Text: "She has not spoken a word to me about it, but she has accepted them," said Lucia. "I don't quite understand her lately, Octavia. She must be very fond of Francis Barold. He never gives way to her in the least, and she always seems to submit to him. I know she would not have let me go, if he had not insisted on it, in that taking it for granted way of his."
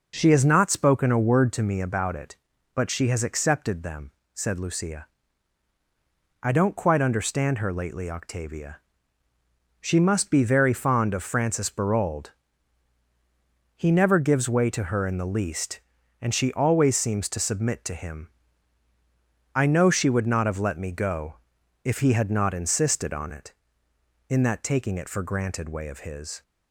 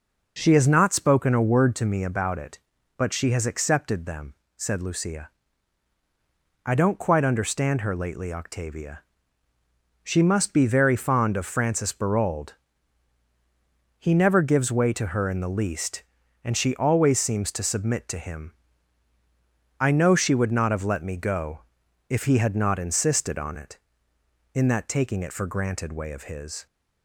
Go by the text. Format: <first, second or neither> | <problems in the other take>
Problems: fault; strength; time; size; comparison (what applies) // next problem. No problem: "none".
neither | none